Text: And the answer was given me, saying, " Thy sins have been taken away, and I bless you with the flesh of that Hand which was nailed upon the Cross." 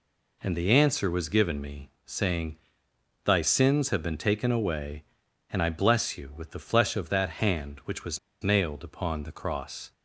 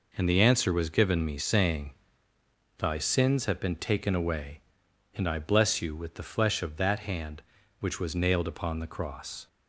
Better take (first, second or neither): second